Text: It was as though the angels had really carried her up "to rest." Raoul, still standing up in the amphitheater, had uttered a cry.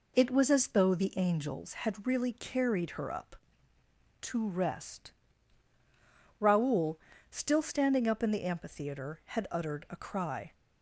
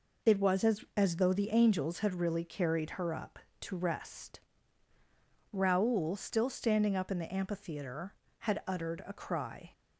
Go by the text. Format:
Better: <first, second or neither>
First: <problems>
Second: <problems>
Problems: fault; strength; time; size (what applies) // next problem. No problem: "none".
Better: first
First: none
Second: says "as" twice; at 0.9 s